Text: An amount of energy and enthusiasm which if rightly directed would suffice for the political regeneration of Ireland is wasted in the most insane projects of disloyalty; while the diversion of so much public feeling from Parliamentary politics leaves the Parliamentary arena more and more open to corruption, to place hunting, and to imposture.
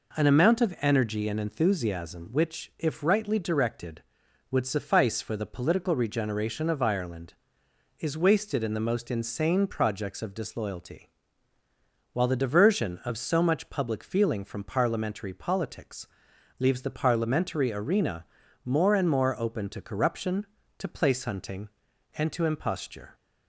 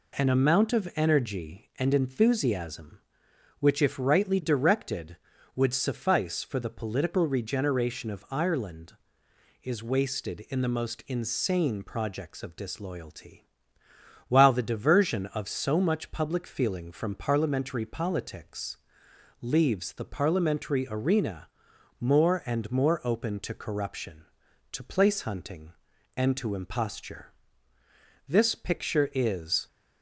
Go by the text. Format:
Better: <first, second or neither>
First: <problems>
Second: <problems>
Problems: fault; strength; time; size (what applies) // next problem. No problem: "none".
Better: first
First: pauses between "politics" and "leaves"; noticeable; at 16.0 s; 0.50 s long // pauses between "arena" and "more"; at 18.2 s; 0.40 s long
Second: pauses between "politics" and "leaves"; noticeable; at 18.7 s; 0.64 s long // pauses between "arena" and "more"; noticeable; at 21.4 s; 0.50 s long // goes on to say "This picture is"; from 28.2 s on; 1.3 s long